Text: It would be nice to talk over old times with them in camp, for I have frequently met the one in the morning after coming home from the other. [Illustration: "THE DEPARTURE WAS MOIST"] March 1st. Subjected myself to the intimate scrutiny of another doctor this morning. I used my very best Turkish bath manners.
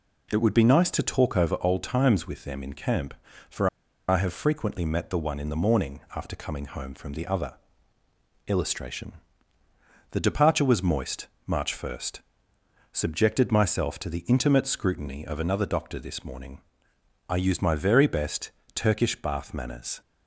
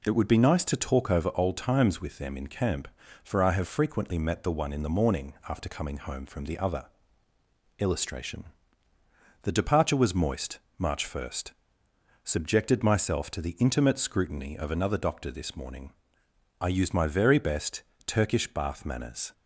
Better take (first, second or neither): second